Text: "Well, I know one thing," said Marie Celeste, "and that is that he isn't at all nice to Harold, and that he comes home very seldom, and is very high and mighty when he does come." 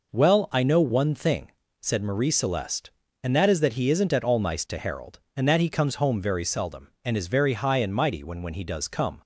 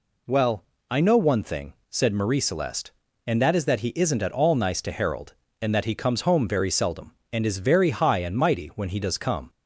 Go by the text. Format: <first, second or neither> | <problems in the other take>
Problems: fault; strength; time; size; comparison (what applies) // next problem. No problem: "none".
second | says "when" twice; at 8.4 s